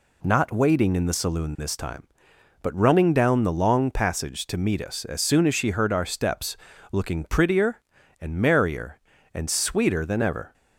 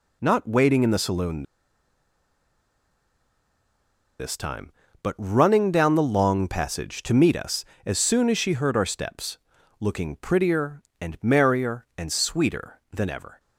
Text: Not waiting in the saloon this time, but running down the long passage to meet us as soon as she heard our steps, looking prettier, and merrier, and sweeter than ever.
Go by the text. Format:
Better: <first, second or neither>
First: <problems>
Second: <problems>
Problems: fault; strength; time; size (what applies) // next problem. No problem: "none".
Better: first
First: none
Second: pauses between "saloon" and "this"; strong; at 1.4 s; 2.7 s long